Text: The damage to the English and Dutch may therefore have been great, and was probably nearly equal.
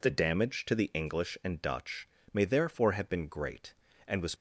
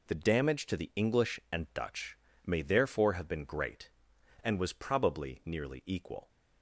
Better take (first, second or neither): second